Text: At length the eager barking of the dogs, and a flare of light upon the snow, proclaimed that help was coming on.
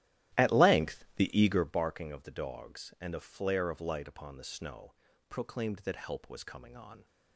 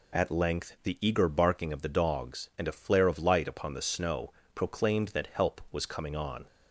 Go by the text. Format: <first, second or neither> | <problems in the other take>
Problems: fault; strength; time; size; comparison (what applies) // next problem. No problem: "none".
second | starts louder than the rest; strong; until 1.8 s; 14 dB